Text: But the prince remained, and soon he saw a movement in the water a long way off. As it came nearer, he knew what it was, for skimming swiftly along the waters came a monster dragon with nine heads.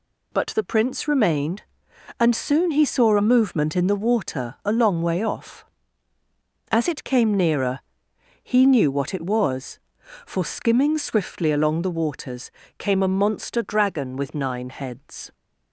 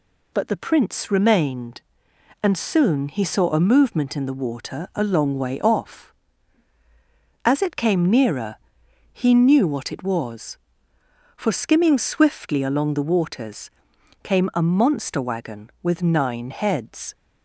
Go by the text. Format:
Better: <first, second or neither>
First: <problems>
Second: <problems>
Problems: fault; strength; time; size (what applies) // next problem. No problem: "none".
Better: first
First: pauses between "waters" and "came"; slight; at 12.5 s; 0.28 s long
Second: pauses between "waters" and "came"; noticeable; at 13.6 s; 0.54 s long // says "wagon" for "dragon"; at 15.2 s